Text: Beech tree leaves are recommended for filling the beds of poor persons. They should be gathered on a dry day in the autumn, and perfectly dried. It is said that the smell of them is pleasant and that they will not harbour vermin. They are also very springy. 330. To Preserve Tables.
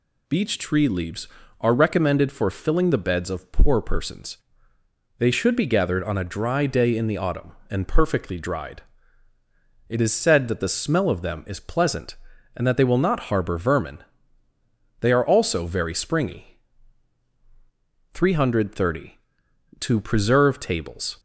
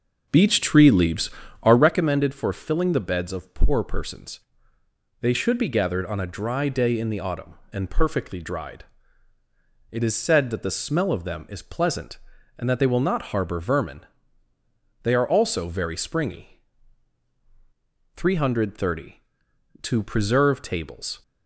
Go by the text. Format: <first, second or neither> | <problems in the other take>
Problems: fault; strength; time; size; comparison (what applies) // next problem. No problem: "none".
first | starts louder than the rest; noticeable; until 2.0 s; 5.5 dB